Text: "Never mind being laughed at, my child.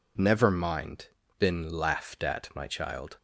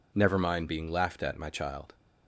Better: second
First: says "been" for "being"; at 1.3 s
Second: none

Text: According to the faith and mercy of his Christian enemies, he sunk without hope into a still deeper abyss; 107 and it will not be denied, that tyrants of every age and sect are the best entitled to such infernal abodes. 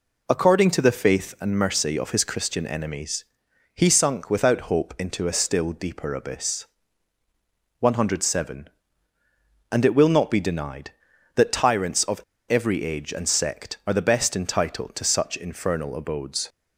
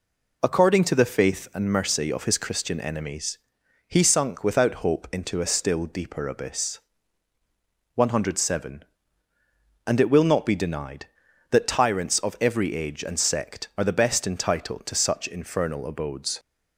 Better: second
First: pauses between "of" and "every"; slight; at 12.2 s; 0.30 s long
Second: none

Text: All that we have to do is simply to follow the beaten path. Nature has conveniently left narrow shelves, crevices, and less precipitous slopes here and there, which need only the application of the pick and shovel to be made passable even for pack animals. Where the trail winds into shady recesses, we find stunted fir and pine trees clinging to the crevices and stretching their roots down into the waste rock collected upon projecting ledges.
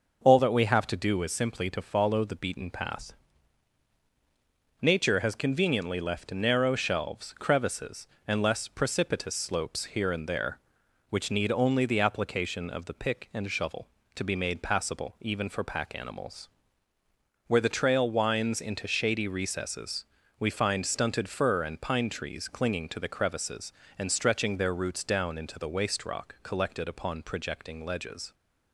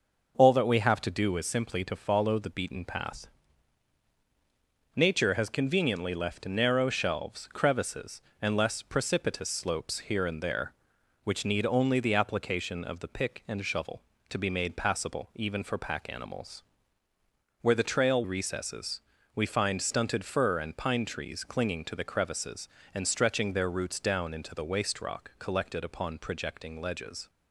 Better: first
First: none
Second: skips "winds into shady"; at 18.2 s

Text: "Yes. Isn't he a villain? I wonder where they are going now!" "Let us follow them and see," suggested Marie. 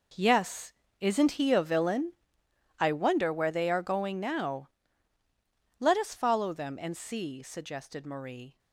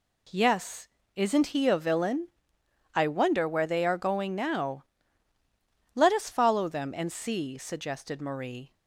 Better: second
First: gets quieter; strong; throughout; 13 dB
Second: none

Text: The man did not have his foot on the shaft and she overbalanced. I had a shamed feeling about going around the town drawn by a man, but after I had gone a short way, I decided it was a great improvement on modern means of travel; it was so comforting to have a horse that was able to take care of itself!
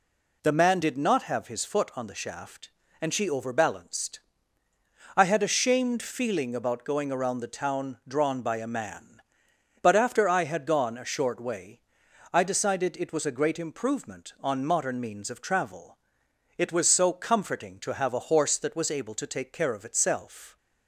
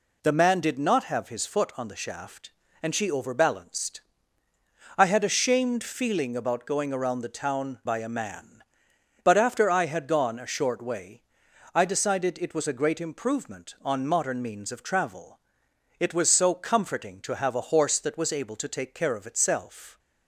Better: first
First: none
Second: skips "drawn"; at 7.8 s

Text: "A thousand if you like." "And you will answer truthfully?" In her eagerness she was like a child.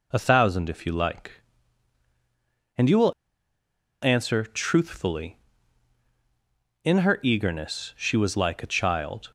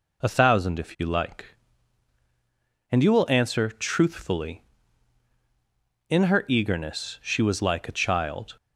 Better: second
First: pauses between "will" and "answer"; noticeable; at 3.1 s; 0.90 s long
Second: none

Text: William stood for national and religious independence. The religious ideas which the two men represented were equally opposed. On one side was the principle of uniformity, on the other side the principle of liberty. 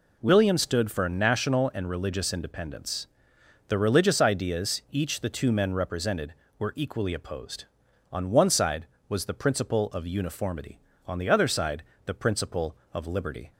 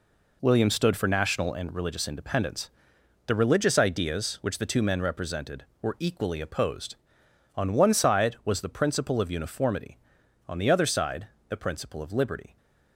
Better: second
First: says "each" for "which"; at 4.9 s // pauses between "side" and "the"; slight; at 11.8 s; 0.22 s long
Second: pauses between "side" and "the"; slight; at 11.2 s; 0.22 s long

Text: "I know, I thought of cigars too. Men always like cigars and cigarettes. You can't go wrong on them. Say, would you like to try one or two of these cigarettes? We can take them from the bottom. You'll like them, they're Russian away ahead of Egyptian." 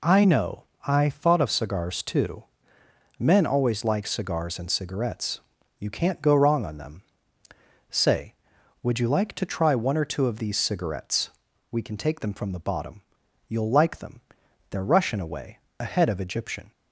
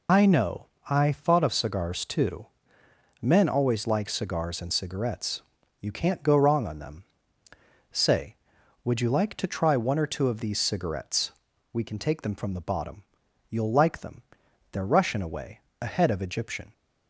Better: first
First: pauses between "away" and "ahead"; slight; at 15.5 s; 0.20 s long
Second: loses the start of "I"; at 0.0 s; 65 ms // pauses between "away" and "ahead"; slight; at 15.6 s; 0.20 s long

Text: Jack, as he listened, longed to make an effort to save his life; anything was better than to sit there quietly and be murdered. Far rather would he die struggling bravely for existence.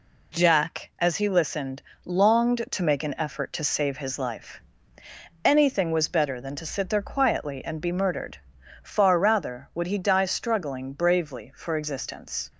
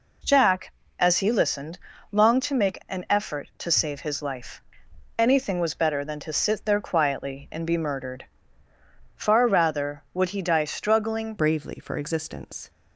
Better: first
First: none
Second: changes voice at "bravely"; from 11.3 s on; 1.3 s long

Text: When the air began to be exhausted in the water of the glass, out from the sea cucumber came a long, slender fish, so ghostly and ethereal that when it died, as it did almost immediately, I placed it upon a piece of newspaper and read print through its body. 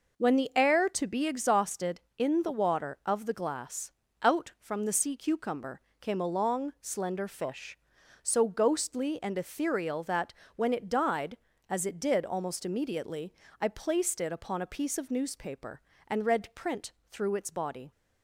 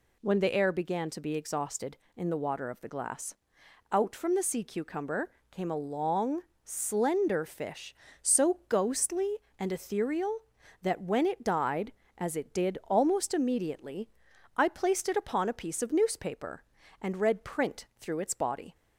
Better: second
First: skips "began"; at 0.8 s // pauses between "cucumber" and "came"; slight; at 5.8 s; 0.18 s long // pauses between "that" and "when"; slight; at 10.3 s; 0.22 s long // pauses between "print" and "through"; slight; at 16.9 s; 0.18 s long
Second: pauses between "cucumber" and "came"; slight; at 5.3 s; 0.22 s long

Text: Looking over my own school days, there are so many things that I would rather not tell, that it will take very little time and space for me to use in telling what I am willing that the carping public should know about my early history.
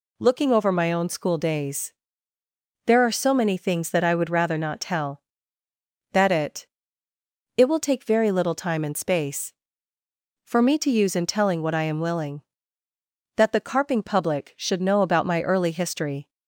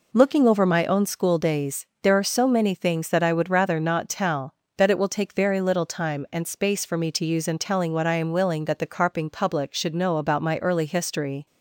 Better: second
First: says "it" twice; at 7.5 s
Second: none

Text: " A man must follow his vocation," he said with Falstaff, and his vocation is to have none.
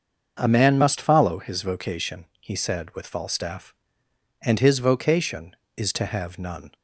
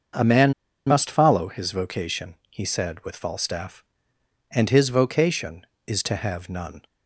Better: first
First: starts louder than the rest; until 1.3 s; 6.5 dB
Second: starts louder than the rest; until 1.4 s; 6.5 dB // pauses between "man" and "must"; slight; at 0.5 s; 0.34 s long

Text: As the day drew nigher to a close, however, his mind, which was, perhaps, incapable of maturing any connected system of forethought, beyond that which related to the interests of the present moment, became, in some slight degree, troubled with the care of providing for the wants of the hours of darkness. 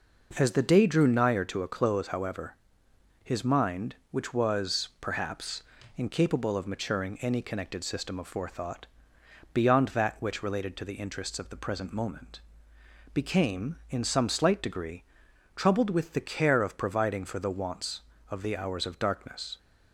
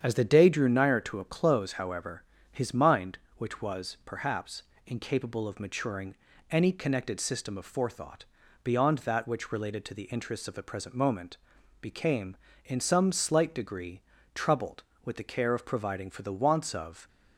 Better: first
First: none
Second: starts louder than the rest; strong; until 1.0 s; 8 dB // pauses between "maturing" and "any"; slight; at 6.1 s; 0.34 s long // stops before "the hours of darkness"; at 17.0 s

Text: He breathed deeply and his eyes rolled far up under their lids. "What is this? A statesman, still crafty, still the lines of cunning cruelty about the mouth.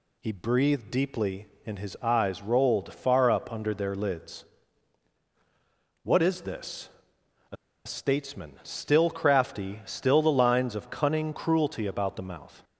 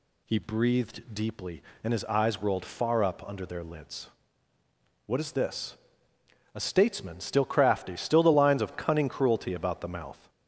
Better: second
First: pauses between "A" and "statesman"; slight; at 7.5 s; 0.30 s long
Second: none

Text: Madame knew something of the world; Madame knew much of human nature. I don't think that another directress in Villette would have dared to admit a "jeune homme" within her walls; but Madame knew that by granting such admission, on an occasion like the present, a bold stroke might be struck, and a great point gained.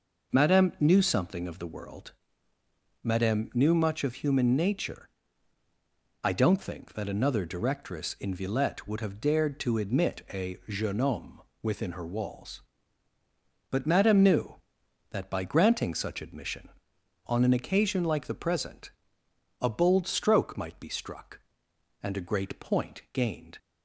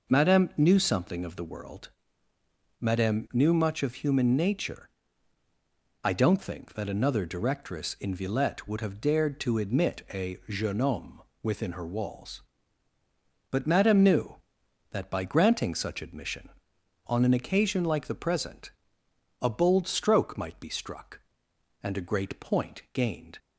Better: neither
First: pauses between "homme" and "within"; slight; at 11.4 s; 0.22 s long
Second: pauses between "homme" and "within"; slight; at 11.2 s; 0.22 s long

